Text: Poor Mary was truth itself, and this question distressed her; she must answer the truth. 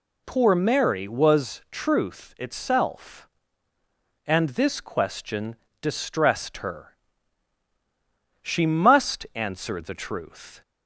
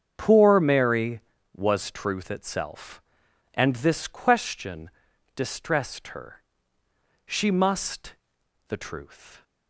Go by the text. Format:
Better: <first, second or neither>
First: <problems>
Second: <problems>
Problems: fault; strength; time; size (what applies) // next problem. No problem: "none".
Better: first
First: pauses between "question" and "distressed"; slight; at 5.5 s; 0.28 s long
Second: starts louder than the rest; strong; until 1.1 s; 7.5 dB // pauses between "question" and "distressed"; at 4.8 s; 0.44 s long // skips "answer"; at 8.4 s